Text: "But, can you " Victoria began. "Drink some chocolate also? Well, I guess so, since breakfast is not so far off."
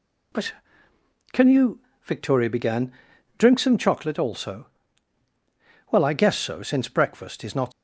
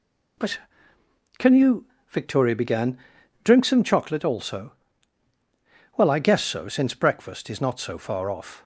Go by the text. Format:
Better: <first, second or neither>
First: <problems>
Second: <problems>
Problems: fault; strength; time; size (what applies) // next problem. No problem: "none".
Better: second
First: stops before "so far off"; at 7.7 s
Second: none